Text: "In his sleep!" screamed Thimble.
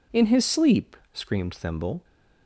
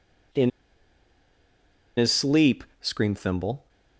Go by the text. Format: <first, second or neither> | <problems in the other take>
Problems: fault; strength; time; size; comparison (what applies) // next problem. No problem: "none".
first | pauses between "In" and "his"; strong; at 0.4 s; 1.4 s long